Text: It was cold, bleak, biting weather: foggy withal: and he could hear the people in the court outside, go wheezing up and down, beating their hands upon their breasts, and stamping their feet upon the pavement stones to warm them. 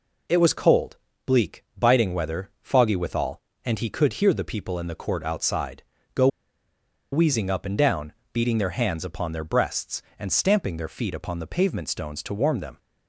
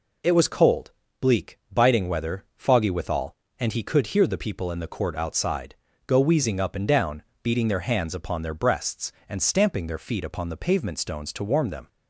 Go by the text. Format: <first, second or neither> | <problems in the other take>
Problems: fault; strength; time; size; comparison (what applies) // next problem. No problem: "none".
second | pauses between "go" and "wheezing"; noticeable; at 6.2 s; 0.84 s long